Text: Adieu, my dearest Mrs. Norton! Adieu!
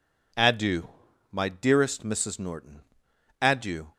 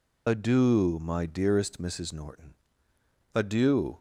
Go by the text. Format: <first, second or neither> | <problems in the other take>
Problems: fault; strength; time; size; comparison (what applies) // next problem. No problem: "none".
first | loses the start of "Adieu"; at 0.2 s; 60 ms